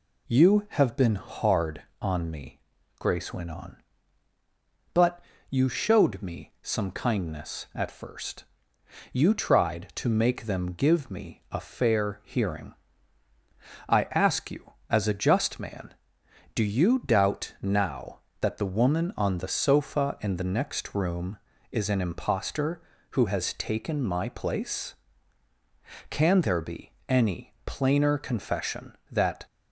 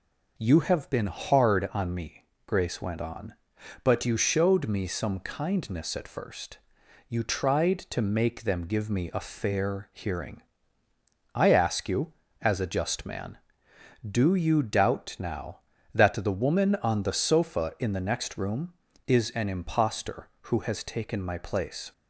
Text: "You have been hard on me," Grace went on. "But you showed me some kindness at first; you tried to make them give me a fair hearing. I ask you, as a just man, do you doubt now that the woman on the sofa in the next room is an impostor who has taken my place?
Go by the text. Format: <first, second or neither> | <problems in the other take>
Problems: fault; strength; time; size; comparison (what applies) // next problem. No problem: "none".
second | pauses between "But" and "you"; slight; at 5.2 s; 0.30 s long // goes on to say "Can there be any plainer confession that"; strong; from 26.0 s on; 3.3 s long